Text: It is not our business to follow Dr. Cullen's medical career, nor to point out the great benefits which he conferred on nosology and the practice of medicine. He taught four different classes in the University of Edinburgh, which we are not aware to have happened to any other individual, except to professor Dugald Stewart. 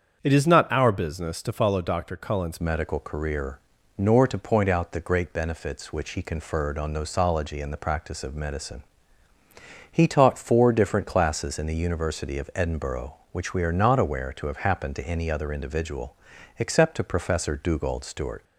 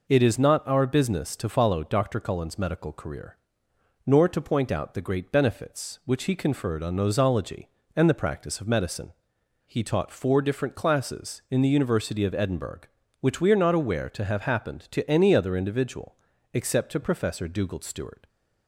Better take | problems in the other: second | starts louder than the rest; until 1.2 s; 7 dB // changes voice at "medical"; from 2.6 s on; 15.8 s long

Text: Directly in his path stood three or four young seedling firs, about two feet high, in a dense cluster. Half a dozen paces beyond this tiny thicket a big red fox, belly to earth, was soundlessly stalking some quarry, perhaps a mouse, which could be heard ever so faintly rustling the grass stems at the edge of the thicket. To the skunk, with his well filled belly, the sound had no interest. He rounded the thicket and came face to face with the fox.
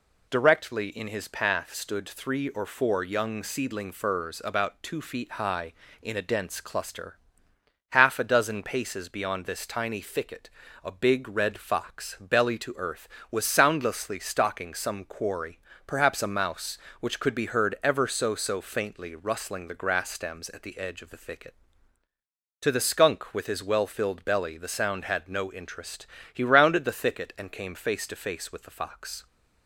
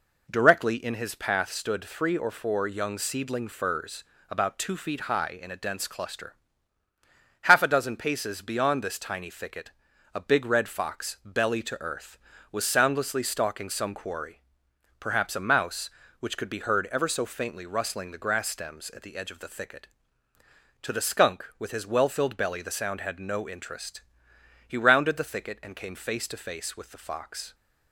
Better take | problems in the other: second | pauses between "thicket" and "a"; slight; at 10.4 s; 0.34 s long; also in the second // says "so" twice; at 18.3 s

